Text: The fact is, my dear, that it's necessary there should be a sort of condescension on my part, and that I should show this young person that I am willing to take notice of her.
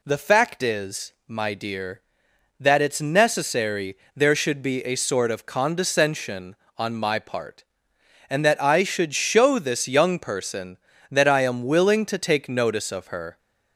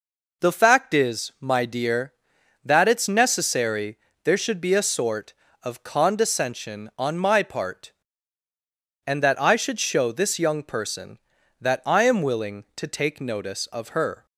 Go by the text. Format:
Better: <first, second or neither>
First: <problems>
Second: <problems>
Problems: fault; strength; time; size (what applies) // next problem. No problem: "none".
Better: neither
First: pauses between "necessary" and "there"; slight; at 3.9 s; 0.20 s long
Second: pauses between "necessary" and "there"; slight; at 3.9 s; 0.26 s long